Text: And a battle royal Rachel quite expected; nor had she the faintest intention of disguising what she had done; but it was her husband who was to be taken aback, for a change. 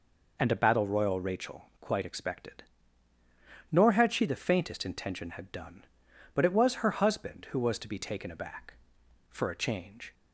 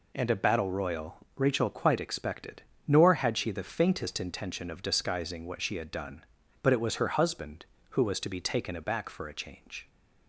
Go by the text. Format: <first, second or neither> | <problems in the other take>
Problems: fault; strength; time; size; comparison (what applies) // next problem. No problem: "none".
second | skips "of disguising what she"; at 5.3 s